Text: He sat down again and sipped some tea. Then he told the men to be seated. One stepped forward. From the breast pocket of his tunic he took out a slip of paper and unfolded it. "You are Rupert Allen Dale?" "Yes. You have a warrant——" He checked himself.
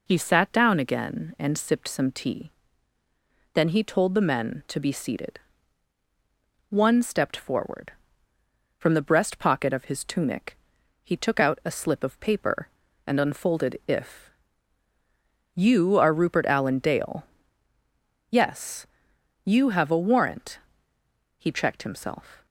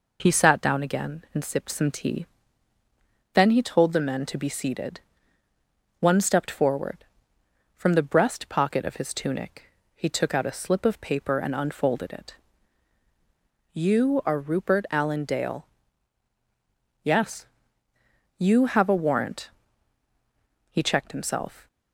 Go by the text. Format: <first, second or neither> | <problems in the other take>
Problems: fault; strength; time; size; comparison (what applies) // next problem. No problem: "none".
second | pauses between "tunic" and "he"; noticeable; at 10.5 s; 0.48 s long; slight in the second // says "if" for "it"; at 13.8 s